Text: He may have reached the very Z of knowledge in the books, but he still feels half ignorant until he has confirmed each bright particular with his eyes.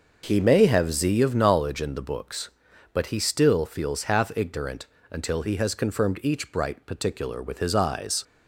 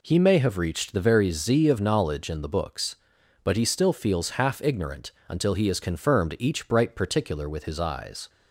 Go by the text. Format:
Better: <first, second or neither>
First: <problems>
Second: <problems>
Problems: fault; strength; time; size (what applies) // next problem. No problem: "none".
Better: second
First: skips "reached the very"; at 0.9 s // pauses between "ignorant" and "until"; slight; at 4.8 s; 0.26 s long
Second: pauses between "ignorant" and "until"; slight; at 5.1 s; 0.16 s long